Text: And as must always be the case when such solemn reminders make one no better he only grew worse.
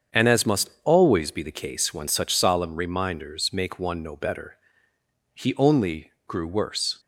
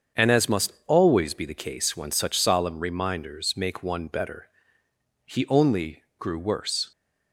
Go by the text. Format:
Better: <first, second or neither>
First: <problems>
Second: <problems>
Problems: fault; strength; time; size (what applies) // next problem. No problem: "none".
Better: first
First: starts louder than the rest; strong; until 1.2 s; 7.5 dB // pauses between "better" and "he"; noticeable; at 4.5 s; 0.76 s long // pauses between "only" and "grew"; slight; at 6.1 s; 0.16 s long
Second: starts louder than the rest; strong; until 1.3 s; 7 dB // skips "no"; at 4.0 s // pauses between "better" and "he"; noticeable; at 4.4 s; 0.76 s long // pauses between "only" and "grew"; slight; at 6.0 s; 0.16 s long